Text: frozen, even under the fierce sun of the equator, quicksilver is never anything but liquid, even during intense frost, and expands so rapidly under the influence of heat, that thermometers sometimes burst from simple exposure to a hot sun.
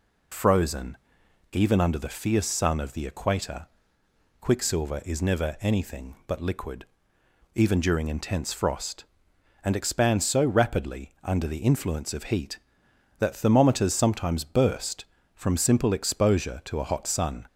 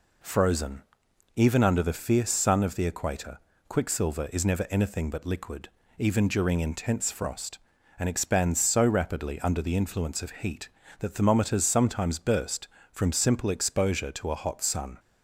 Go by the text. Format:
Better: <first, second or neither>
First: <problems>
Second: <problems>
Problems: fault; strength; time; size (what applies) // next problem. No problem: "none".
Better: neither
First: none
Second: none